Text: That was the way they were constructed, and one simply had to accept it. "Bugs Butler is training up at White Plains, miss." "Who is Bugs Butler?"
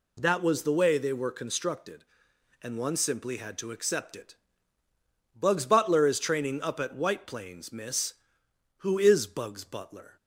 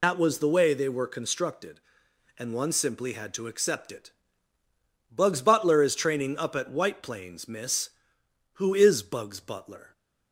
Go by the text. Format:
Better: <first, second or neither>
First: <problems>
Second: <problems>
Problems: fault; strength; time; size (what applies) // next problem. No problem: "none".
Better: first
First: none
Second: loses the start of "That"; at 0.0 s; 100 ms